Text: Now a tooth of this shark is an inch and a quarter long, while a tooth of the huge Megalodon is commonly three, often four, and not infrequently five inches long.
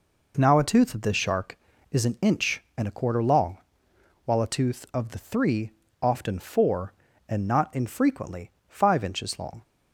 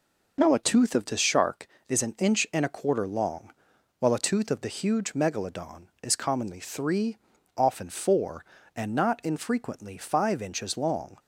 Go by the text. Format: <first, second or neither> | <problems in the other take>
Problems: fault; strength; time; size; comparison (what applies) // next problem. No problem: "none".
second | skips "huge Megalodon is commonly"; at 5.1 s // pauses between "infrequently" and "five"; slight; at 8.4 s; 0.18 s long